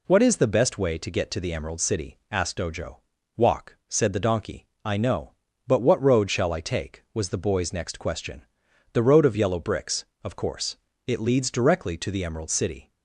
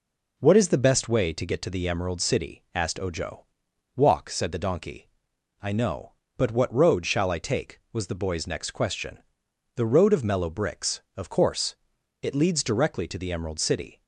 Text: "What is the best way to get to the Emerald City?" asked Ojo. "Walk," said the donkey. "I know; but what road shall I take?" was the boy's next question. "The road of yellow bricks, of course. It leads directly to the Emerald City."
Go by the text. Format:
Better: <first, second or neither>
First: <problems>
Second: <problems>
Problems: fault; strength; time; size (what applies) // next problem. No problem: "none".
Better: first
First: none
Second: says "mellow" for "yellow"; at 10.2 s